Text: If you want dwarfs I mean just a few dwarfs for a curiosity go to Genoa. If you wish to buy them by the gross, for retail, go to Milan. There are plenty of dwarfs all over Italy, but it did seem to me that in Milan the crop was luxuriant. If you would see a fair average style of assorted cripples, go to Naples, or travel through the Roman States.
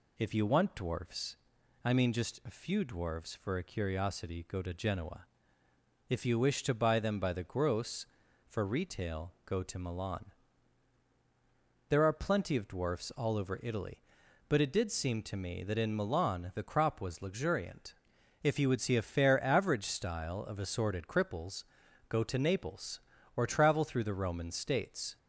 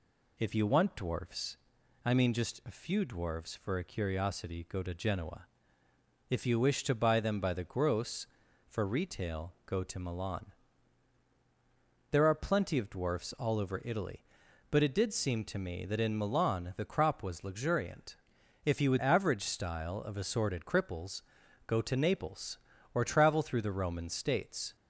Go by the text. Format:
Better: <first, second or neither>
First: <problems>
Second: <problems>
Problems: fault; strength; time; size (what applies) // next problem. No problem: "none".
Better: first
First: pauses between "dwarfs" and "I"; noticeable; at 1.3 s; 0.48 s long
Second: pauses between "dwarfs" and "I"; noticeable; at 1.5 s; 0.48 s long // skips "see a fair"; at 19.0 s